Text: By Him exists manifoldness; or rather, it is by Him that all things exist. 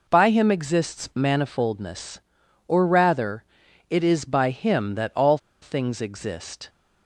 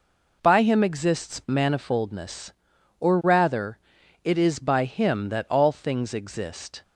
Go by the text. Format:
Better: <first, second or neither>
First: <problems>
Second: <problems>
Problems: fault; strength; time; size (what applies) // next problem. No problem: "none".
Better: second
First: pauses between "all" and "things"; slight; at 5.3 s; 0.24 s long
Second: none